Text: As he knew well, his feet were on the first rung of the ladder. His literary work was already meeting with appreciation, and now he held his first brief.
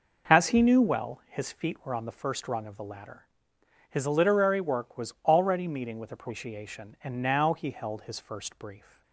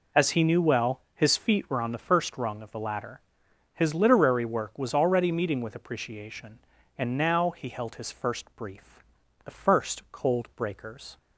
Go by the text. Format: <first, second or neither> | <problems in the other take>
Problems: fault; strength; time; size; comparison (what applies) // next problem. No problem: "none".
first | goes on to say "The first cold breakers"; strong; from 9.4 s on; 1.7 s long